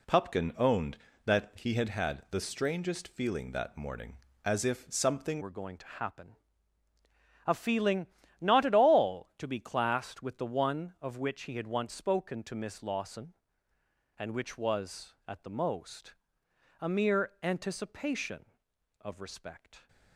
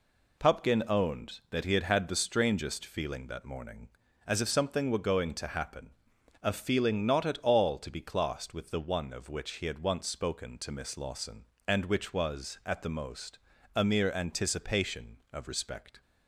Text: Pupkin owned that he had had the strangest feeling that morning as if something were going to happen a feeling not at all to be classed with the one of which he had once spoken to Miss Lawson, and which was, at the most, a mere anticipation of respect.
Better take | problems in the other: second | changes voice at "were"; from 5.3 s on; 14.5 s long // pauses between "happen" and "a"; at 6.3 s; 1.1 s long; noticeable in the second // pauses between "feeling" and "not"; slight; at 8.0 s; 0.34 s long

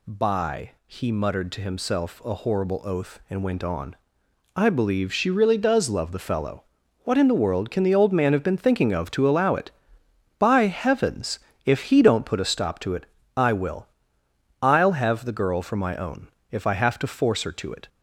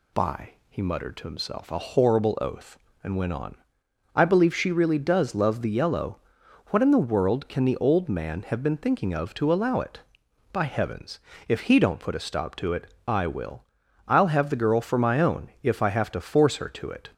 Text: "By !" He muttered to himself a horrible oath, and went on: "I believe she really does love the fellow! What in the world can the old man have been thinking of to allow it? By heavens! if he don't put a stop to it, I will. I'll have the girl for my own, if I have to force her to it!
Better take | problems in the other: first | says "yellow" for "fellow"; at 5.6 s

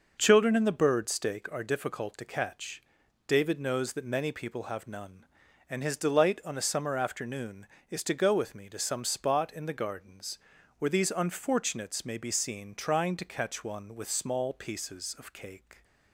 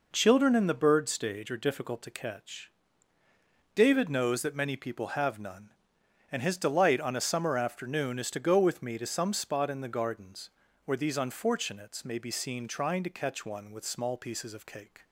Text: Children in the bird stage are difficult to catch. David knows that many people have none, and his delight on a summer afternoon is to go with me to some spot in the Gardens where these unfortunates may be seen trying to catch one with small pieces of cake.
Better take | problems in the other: second | says "stake" for "stage"; at 1.0 s // pauses between "Gardens" and "where"; at 10.3 s; 0.40 s long; slight in the second

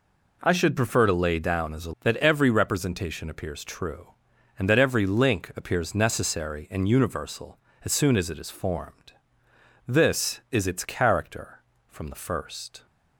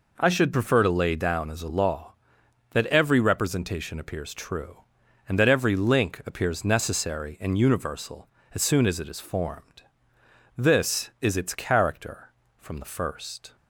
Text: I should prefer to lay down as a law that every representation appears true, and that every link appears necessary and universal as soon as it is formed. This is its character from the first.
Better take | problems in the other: second | skips "law"; at 1.9 s

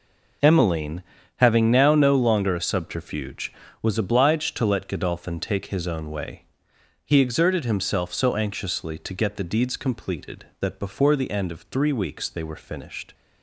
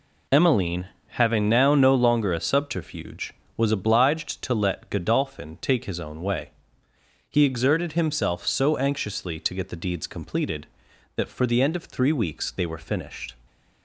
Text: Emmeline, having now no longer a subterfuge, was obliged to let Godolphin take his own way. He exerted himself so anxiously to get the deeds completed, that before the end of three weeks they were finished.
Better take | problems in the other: first | says "for" for "before"; at 11.2 s

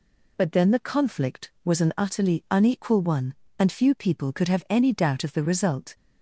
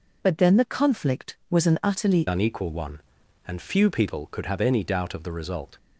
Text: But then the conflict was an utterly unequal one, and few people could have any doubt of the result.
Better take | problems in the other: first | changes voice at "unequal"; from 2.2 s on; 3.5 s long

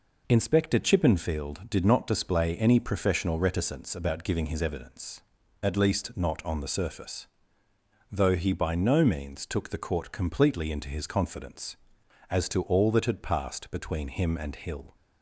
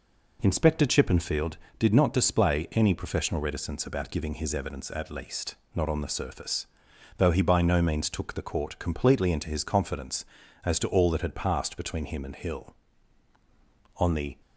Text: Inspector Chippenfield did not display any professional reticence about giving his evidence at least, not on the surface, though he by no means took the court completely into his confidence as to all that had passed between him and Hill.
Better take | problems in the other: first | goes on to say "On the"; slight; from 13.9 s on; 0.42 s long

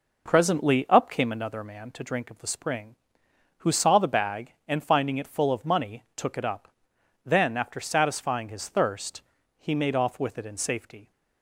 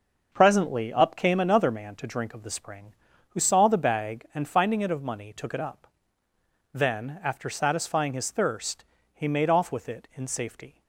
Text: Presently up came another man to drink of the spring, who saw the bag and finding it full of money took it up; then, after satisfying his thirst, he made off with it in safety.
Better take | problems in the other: first | starts louder than the rest; noticeable; until 1.3 s; 6 dB // skips "full"; at 4.8 s

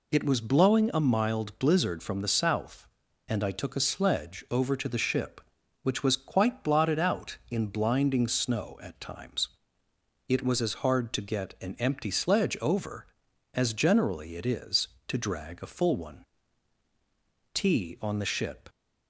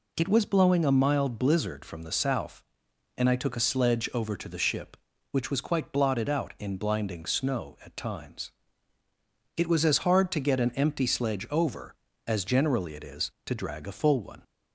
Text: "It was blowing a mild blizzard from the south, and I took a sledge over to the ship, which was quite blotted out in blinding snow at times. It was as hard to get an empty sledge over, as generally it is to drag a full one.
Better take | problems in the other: second | goes on to say "Tea on the ship"; noticeable; from 17.5 s on; 1.0 s long

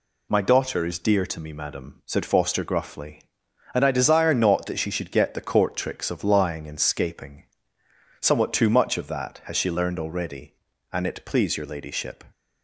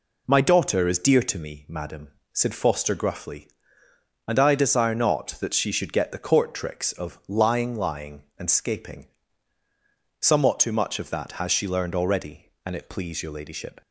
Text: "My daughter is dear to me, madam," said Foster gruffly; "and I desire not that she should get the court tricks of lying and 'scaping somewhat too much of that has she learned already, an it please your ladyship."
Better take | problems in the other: first | says "lying" twice; at 7.7 s // pauses between "scaping" and "somewhat"; at 9.0 s; 1.1 s long; noticeable in the first

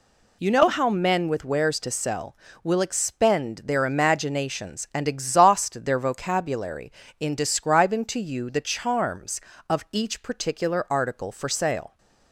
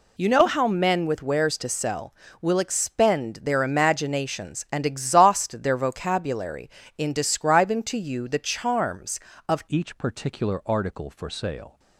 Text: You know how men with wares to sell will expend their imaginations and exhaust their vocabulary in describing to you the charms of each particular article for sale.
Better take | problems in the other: first | changes voice at "each"; from 9.6 s on; 2.1 s long

